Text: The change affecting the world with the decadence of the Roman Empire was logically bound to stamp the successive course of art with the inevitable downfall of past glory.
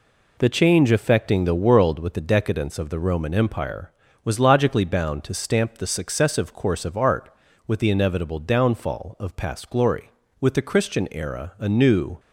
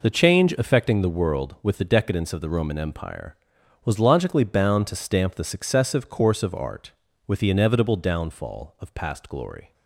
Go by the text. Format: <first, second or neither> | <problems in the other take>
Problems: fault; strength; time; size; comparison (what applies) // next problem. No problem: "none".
second | goes on to say "With the Christian era a new"; strong; from 10.3 s on; 1.8 s long